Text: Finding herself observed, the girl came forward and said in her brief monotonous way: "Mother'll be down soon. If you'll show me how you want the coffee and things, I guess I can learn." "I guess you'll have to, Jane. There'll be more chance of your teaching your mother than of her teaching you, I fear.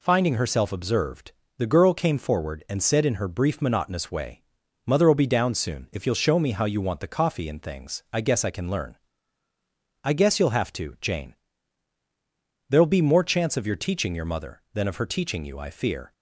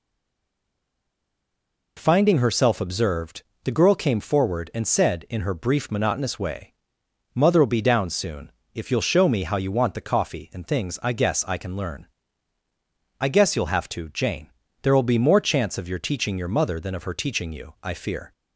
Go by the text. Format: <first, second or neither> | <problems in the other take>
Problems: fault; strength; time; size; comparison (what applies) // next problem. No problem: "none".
first | stays silent before the first word; noticeable; until 1.9 s; 1.9 s long